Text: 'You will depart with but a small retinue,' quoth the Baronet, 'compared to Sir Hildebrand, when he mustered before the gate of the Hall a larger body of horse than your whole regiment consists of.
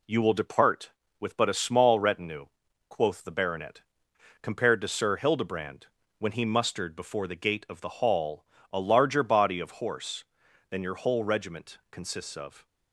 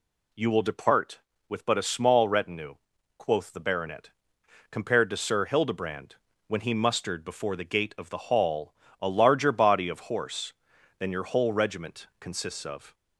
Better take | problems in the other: second | gets quieter; slight; throughout; 2.5 dB // pauses between "Hall" and "a"; slight; at 8.4 s; 0.28 s long; slight in the second

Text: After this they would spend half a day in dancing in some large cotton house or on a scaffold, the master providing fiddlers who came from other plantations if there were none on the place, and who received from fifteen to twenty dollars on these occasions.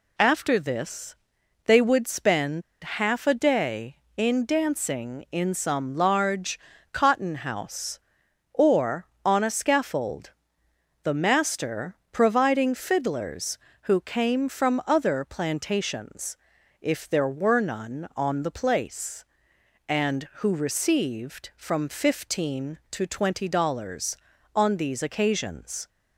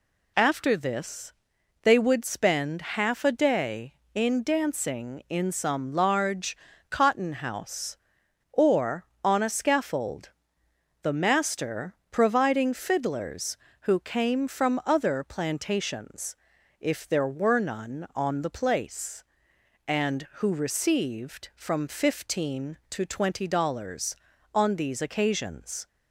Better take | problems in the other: second | pauses between "this" and "they"; noticeable; at 1.1 s; 0.50 s long; noticeable in the second // pauses between "spend" and "half"; slight; at 2.6 s; 0.22 s long // pauses between "large" and "cotton"; slight; at 6.5 s; 0.34 s long; slight in the second // pauses between "master" and "providing"; slight; at 11.9 s; 0.16 s long; slight in the second // pauses between "plantations" and "if"; at 16.3 s; 0.44 s long; also in the second

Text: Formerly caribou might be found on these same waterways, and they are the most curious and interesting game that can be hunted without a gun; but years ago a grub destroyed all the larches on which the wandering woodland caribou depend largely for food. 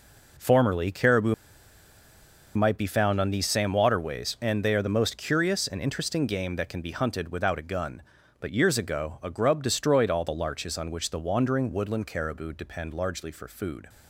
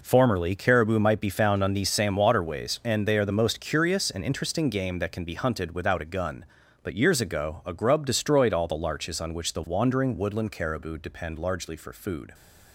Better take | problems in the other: second | pauses between "caribou" and "might"; at 1.3 s; 1.2 s long

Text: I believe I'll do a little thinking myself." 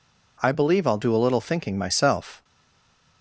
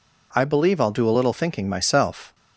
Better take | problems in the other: second | stays silent after the last word; slight; from 2.4 s on; 0.8 s long

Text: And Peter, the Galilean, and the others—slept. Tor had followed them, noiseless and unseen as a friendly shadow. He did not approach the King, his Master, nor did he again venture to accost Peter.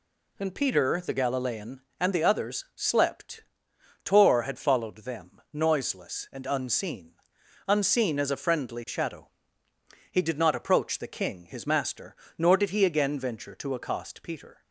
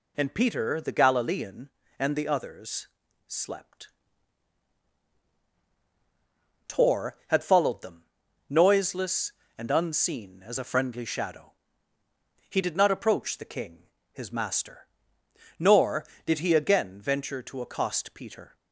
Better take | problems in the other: second | says "unseen" twice; at 7.6 s

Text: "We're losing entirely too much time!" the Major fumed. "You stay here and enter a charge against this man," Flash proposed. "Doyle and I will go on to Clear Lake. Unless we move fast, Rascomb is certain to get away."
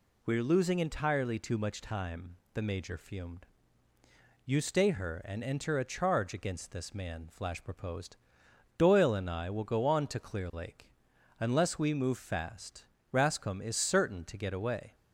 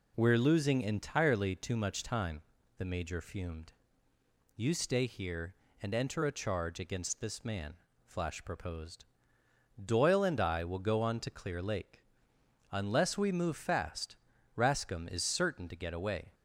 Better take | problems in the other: second | says "her" for "here"; at 4.8 s

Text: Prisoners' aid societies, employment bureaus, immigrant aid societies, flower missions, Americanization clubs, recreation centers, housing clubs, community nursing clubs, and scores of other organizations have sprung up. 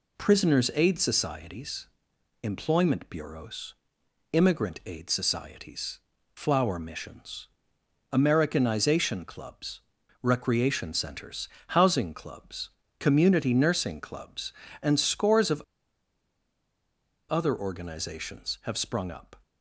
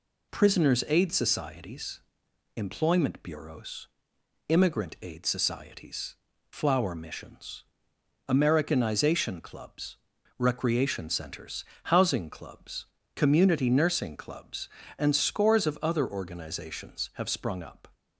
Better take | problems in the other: second | pauses between "of" and "other"; strong; at 15.6 s; 1.6 s long

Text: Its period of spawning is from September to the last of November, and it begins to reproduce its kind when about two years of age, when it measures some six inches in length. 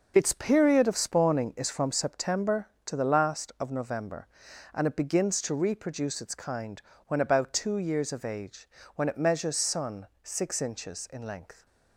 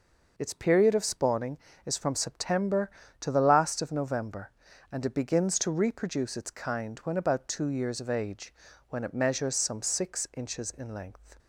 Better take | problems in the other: second | pauses between "kind" and "when"; slight; at 6.8 s; 0.28 s long // says "sun" for "some"; at 9.5 s

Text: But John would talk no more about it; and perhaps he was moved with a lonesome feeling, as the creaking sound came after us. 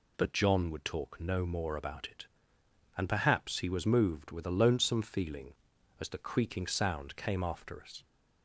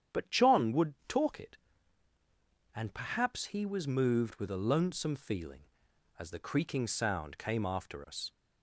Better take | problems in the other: first | starts louder than the rest; strong; until 1.2 s; 9 dB // skips "no more about"; at 1.3 s

